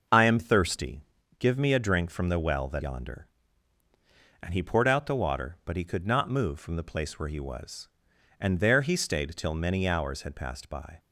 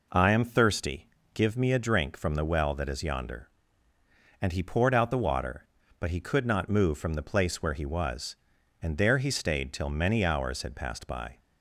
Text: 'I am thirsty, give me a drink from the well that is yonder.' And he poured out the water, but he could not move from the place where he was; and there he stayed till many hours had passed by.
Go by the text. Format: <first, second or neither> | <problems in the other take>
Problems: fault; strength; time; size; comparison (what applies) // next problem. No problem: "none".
second | skips "is"; at 2.8 s